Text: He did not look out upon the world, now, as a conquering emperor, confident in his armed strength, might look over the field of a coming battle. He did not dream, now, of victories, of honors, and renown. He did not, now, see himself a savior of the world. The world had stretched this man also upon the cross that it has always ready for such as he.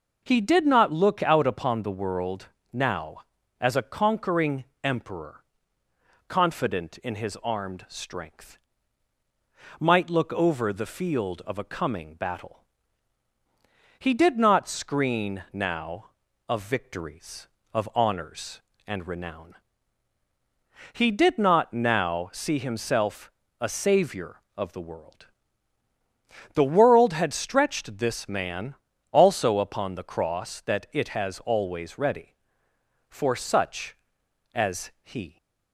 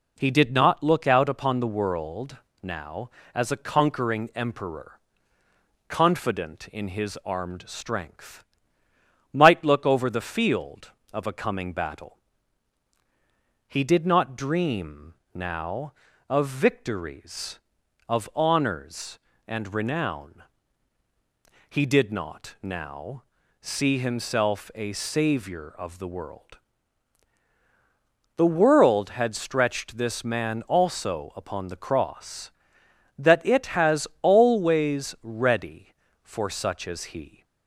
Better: second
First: pauses between "conquering" and "emperor"; slight; at 4.6 s; 0.18 s long // says "screen" for "dream"; at 14.6 s // pauses between "himself" and "a"; slight; at 23.3 s; 0.28 s long // pauses between "man" and "also"; slight; at 28.7 s; 0.36 s long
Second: none

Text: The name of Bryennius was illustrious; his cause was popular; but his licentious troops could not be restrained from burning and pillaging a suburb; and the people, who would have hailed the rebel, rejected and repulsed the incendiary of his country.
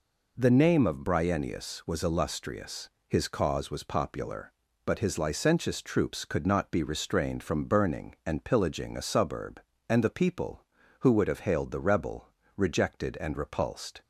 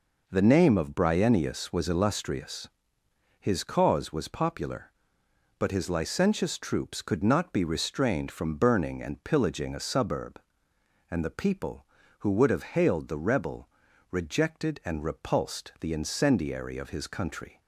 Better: second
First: stops before "the incendiary of his country"; at 14.0 s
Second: none

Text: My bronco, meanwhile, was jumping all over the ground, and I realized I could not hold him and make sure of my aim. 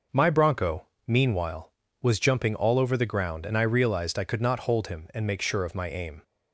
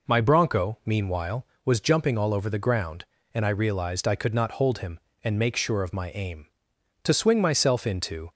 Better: first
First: none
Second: goes on to say "To swing myself into"; noticeable; from 7.0 s on; 1.2 s long

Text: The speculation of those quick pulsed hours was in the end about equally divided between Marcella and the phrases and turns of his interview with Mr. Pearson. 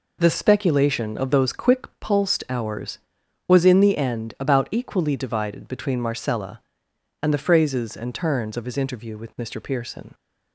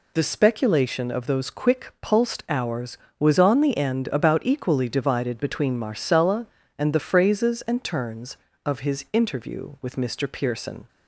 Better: first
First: none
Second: says "on" for "in"; at 3.3 s

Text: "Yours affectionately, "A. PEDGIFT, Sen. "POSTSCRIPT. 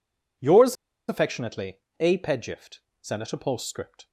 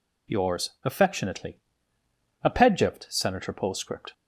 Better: second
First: pauses between "Yours" and "affectionately"; slight; at 0.7 s; 0.34 s long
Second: none

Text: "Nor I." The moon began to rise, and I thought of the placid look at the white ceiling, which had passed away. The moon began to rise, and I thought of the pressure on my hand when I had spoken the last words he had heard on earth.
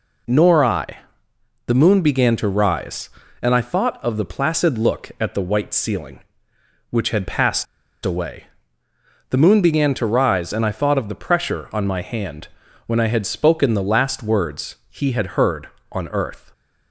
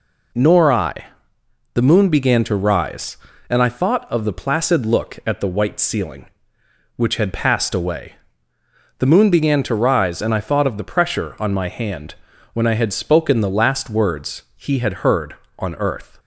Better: second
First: pauses between "passed" and "away"; at 7.6 s; 0.38 s long // pauses between "hand" and "when"; at 12.4 s; 0.38 s long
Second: pauses between "hand" and "when"; at 12.1 s; 0.38 s long

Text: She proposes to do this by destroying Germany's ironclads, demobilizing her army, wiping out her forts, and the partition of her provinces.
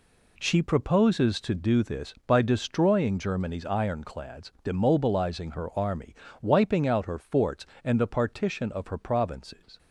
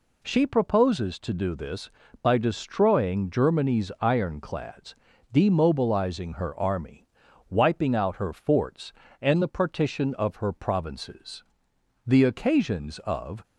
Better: first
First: none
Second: goes on to say "The occasions of"; from 12.0 s on; 1.3 s long

